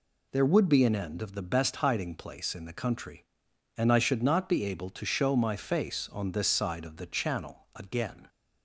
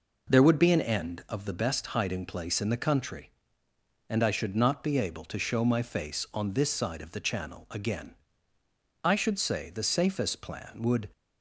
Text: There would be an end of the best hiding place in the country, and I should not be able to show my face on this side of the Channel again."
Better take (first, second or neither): first